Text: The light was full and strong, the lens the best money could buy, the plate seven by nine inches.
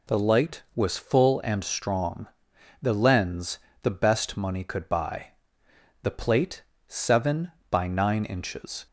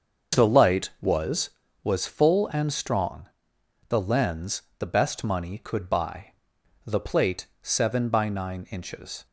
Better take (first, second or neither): first